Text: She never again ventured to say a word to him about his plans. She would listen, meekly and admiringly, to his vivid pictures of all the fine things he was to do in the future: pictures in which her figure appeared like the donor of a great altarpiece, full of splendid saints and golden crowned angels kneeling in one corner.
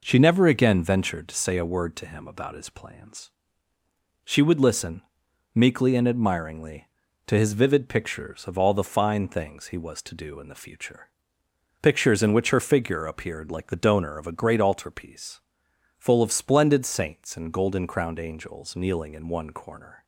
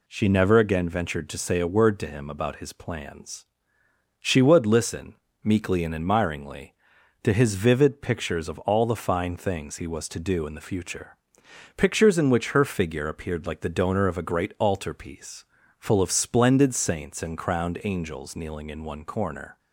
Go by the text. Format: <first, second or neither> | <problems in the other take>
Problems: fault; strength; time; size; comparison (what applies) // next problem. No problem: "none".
first | skips "golden"; at 17.3 s